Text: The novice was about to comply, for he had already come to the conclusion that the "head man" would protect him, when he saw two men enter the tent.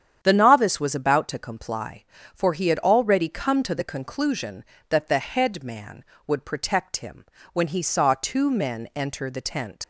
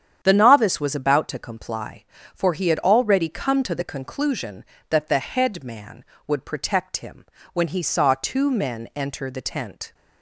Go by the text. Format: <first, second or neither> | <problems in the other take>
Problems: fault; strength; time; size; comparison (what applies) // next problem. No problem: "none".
second | starts louder than the rest; strong; until 1.2 s; 9 dB; strong in the second // leaves "tent" unfinished; at 9.8 s; 95 ms